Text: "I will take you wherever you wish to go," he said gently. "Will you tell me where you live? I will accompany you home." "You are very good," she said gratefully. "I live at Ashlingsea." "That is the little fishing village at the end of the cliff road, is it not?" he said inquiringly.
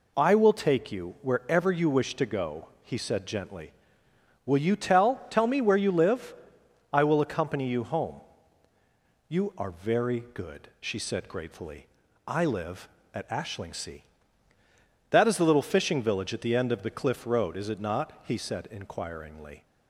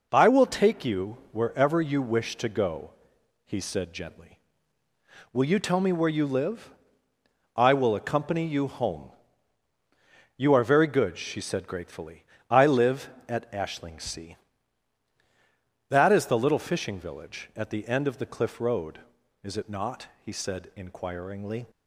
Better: second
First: says "tell" twice; at 5.2 s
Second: none

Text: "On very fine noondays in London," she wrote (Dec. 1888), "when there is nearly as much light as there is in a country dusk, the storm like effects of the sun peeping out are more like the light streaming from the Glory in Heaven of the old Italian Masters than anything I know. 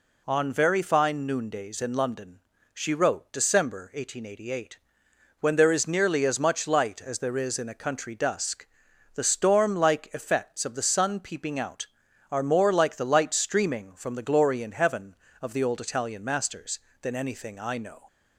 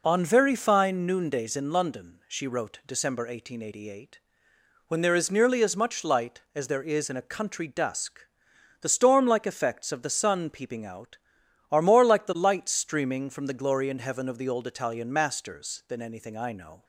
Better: neither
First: none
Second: none

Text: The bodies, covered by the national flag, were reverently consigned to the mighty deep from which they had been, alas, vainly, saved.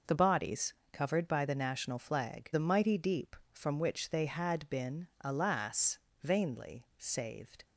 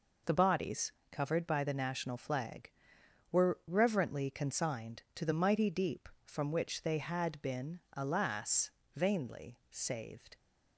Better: second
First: skips "were reverently consigned to"; at 2.5 s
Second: none

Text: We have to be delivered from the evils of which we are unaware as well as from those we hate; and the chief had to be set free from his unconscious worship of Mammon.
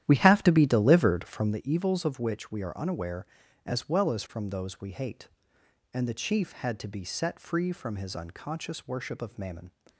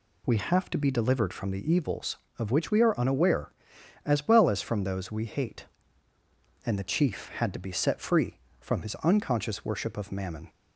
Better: second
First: starts louder than the rest; strong; until 1.6 s; 11.5 dB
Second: none

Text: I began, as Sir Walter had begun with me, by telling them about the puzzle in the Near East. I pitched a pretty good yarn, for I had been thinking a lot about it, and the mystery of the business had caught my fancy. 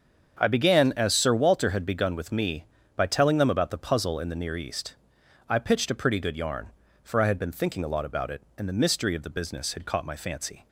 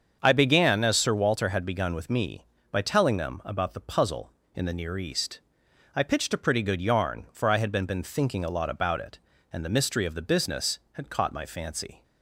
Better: first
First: starts louder than the rest; until 1.4 s; 7 dB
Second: starts louder than the rest; until 1.2 s; 7 dB // says "been" twice; at 7.8 s

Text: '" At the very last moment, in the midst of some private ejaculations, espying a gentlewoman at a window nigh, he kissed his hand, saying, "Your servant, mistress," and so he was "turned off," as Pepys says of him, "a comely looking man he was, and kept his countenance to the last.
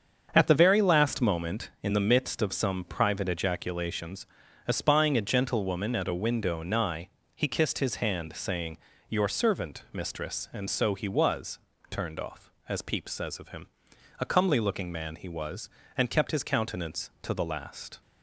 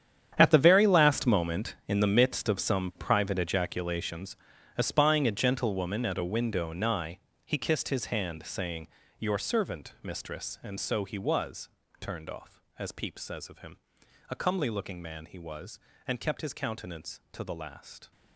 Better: first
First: starts louder than the rest; strong; until 1.3 s; 7 dB // pauses between "was" and "turned"; slight; at 11.5 s; 0.32 s long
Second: gets quieter; strong; throughout; 14.5 dB // starts louder than the rest; strong; until 1.3 s; 9 dB // pauses between "was" and "turned"; slight; at 11.6 s; 0.32 s long

